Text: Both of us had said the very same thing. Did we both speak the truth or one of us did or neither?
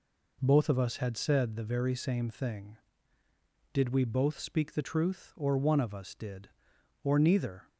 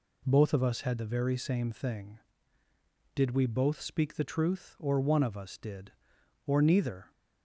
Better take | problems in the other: first | skips "said"; at 0.9 s

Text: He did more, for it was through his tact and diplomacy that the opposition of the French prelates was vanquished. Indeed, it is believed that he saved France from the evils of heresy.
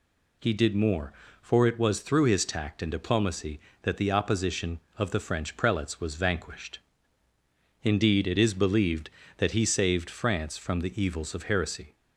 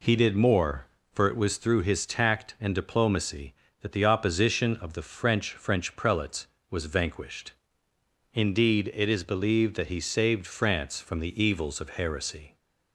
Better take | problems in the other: first | says "French" twice; at 5.5 s

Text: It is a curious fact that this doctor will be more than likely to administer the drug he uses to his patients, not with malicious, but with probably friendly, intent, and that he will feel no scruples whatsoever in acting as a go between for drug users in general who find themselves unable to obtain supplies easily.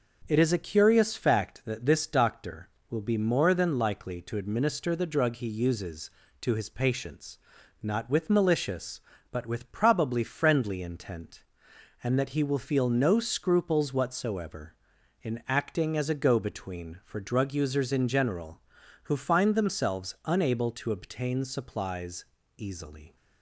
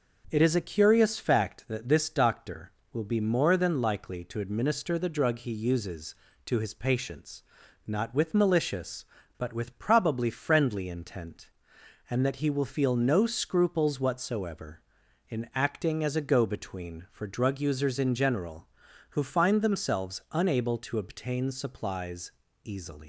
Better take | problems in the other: first | starts louder than the rest; until 1.3 s; 6 dB; also in the first // pauses between "supplies" and "easily"; slight; at 22.3 s; 0.32 s long; slight in the first // leaves "easily" unfinished; at 23.0 s; 135 ms

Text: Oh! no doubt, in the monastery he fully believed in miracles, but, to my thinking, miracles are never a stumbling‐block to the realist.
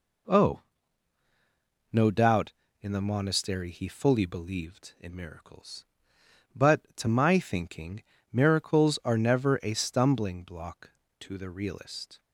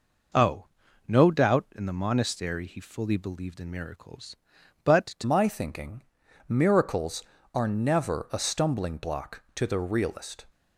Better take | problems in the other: first | changes voice at "my"; from 5.2 s on; 5.2 s long

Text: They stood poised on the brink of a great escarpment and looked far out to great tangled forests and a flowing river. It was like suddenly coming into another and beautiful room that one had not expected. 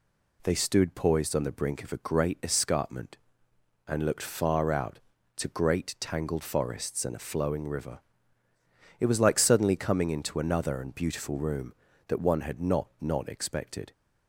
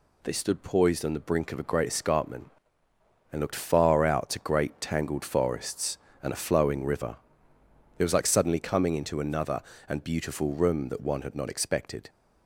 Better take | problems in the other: second | says "not" twice; at 12.9 s

